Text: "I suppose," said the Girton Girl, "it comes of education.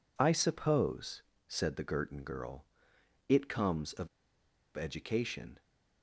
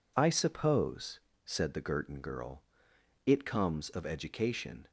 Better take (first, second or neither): second